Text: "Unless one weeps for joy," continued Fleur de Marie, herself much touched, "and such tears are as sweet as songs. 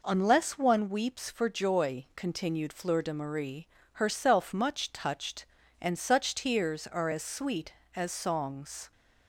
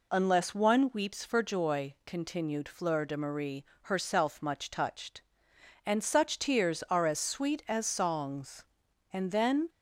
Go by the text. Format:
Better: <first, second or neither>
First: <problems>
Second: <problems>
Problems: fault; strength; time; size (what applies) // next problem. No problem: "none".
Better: first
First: none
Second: goes on to say "And then"; from 9.1 s on; 0.56 s long